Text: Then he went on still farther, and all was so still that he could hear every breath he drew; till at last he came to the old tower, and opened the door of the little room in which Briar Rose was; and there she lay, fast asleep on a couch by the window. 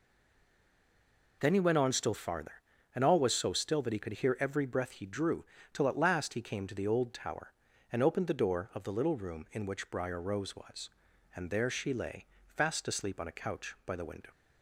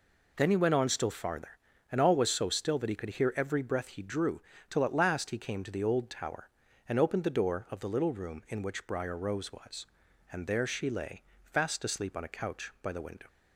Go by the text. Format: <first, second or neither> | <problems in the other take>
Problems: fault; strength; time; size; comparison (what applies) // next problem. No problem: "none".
second | stays silent before the first word; noticeable; until 1.4 s; 1.4 s long